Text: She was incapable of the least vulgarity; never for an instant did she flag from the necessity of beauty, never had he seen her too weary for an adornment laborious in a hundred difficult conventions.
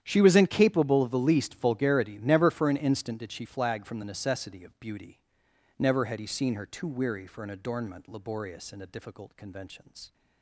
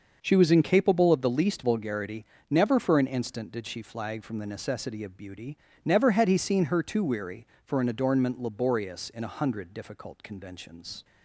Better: second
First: starts louder than the rest; strong; until 1.0 s; 10 dB // skips "hundred"; at 8.8 s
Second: starts louder than the rest; noticeable; until 1.2 s; 6 dB

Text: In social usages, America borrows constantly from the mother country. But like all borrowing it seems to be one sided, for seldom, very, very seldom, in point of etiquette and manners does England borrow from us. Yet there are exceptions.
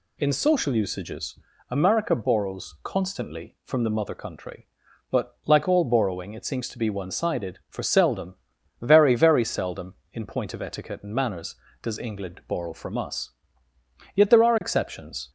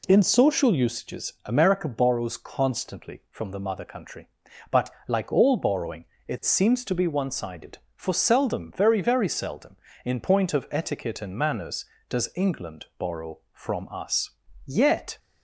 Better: first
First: none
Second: pauses between "But" and "like"; slight; at 4.9 s; 0.16 s long // pauses between "borrowing" and "it"; slight; at 6.0 s; 0.22 s long // stops before "there are exceptions"; at 15.1 s

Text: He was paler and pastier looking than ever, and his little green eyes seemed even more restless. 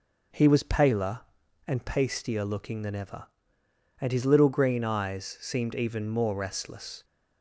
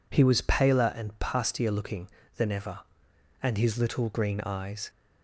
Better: first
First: none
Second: stops before "seemed even more restless"; at 4.8 s

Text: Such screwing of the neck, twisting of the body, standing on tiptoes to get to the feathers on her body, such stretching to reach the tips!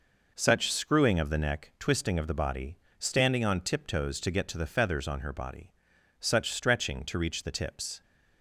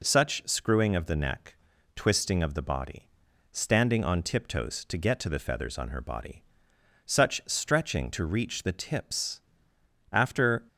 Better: first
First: none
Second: goes on to say "After"; from 10.1 s on; 0.54 s long

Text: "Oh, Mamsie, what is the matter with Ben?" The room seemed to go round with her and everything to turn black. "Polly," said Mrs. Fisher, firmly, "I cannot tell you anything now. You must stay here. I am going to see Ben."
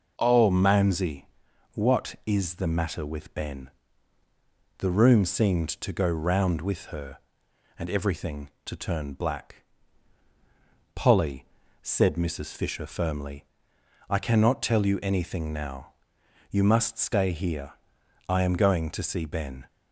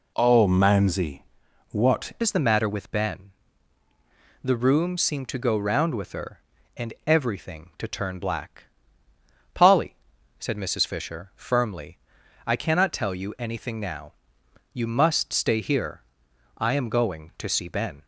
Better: first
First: none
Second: changes voice at "is"; from 2.2 s on; 15.8 s long

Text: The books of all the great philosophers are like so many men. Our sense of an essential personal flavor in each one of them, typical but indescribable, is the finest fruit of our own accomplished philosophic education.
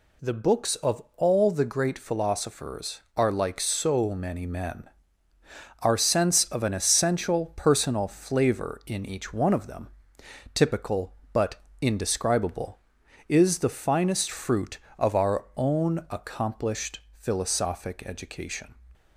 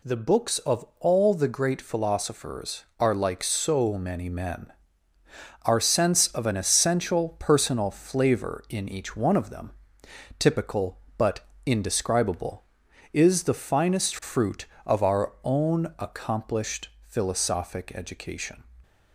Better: neither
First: pauses between "but" and "indescribable"; slight; at 11.6 s; 0.18 s long // pauses between "accomplished" and "philosophic"; slight; at 17.0 s; 0.18 s long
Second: pauses between "but" and "indescribable"; slight; at 11.4 s; 0.18 s long // pauses between "accomplished" and "philosophic"; slight; at 16.8 s; 0.18 s long

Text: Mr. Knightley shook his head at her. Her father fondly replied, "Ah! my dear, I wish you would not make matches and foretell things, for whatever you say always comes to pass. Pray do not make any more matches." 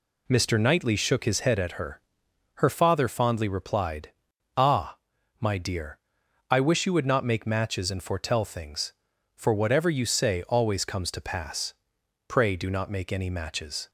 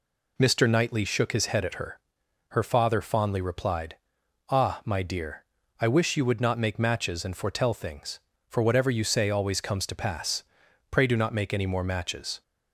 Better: second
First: skips "more"; at 13.2 s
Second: none

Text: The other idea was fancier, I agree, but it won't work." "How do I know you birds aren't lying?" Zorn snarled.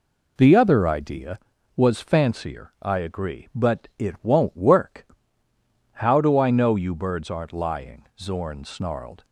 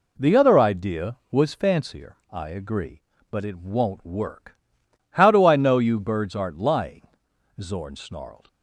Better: neither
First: none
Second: none

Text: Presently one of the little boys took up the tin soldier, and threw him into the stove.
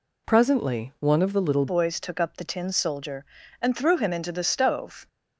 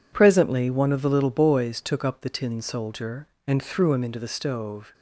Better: second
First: changes voice at "boys"; from 1.6 s on; 3.4 s long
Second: none

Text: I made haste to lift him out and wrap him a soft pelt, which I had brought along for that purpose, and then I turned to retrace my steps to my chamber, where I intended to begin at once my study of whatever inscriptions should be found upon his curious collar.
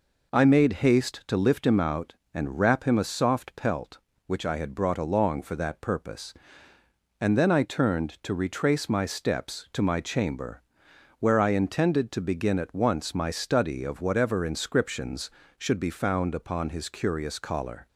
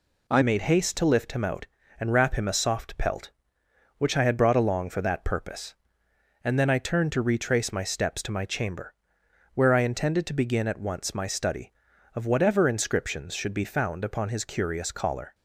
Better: first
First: none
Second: changes voice at "made"; from 0.4 s on; 14.9 s long

